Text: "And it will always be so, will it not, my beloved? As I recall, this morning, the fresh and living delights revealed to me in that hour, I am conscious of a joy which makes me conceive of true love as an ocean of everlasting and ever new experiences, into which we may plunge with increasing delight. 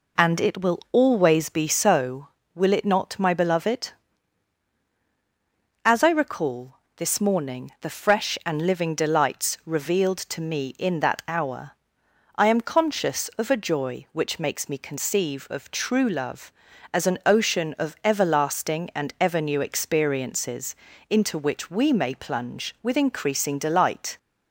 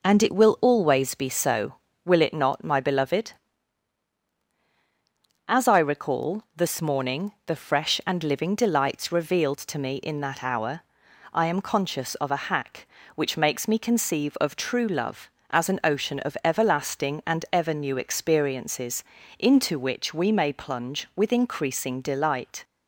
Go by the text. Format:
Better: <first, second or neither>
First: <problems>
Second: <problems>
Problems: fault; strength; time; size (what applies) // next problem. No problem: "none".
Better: first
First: none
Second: says "hack" for "joy"; at 12.4 s